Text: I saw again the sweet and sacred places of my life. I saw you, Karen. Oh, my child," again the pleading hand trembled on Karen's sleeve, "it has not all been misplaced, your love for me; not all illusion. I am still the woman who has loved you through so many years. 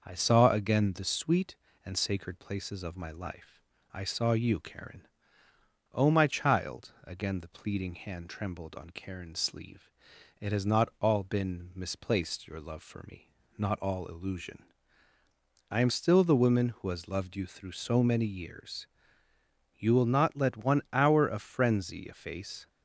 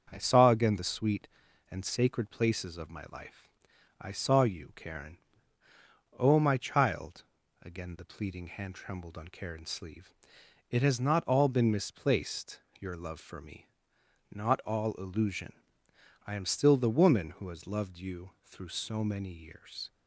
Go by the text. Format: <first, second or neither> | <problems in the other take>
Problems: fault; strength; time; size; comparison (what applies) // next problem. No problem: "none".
second | starts louder than the rest; noticeable; until 1.0 s; 6 dB; also in the second // goes on to say "You will not let one hour of frenzy efface"; strong; from 19.7 s on; 2.9 s long